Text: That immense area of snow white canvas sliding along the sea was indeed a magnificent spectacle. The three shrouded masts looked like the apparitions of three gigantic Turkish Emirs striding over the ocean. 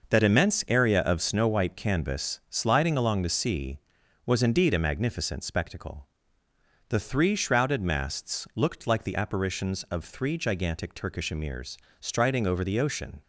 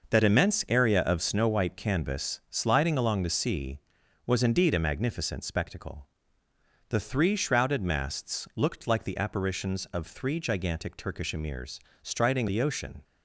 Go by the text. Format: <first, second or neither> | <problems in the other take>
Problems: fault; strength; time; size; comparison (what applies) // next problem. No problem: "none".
first | pauses between "Emirs" and "striding"; slight; at 11.8 s; 0.22 s long; slight in the first // skips "over"; at 12.4 s